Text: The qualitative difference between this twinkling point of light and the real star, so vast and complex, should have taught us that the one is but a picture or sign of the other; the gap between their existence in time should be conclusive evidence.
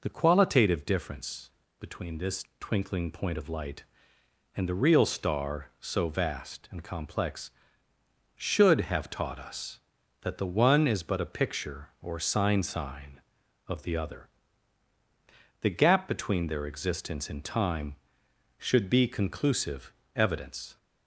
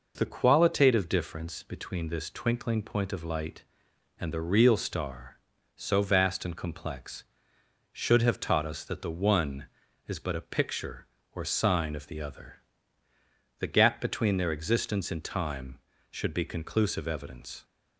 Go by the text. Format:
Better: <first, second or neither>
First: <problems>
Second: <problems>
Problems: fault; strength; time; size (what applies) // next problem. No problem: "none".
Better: second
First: pauses between "difference" and "between"; slight; at 1.5 s; 0.28 s long // says "sign" twice; at 12.6 s // pauses between "conclusive" and "evidence"; slight; at 19.9 s; 0.24 s long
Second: none